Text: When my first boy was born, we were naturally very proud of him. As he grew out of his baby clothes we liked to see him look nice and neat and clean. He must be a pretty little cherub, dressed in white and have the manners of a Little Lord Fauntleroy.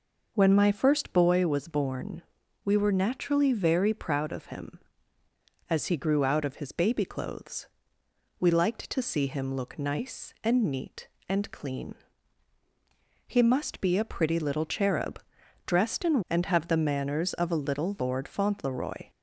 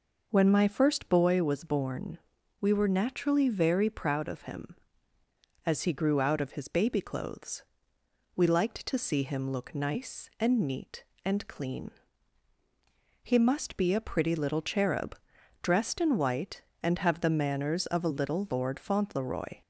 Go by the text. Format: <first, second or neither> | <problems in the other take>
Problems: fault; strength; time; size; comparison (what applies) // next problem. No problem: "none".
second | pauses between "clothes" and "we"; noticeable; at 7.6 s; 0.74 s long; noticeable in the second // skips "white"; at 16.2 s